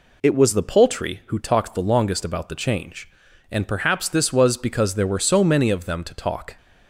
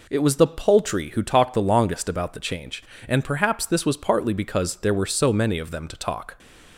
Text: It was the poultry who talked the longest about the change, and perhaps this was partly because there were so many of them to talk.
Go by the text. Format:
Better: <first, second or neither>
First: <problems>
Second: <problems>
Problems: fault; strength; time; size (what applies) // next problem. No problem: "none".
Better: second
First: skips "partly"; at 4.5 s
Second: none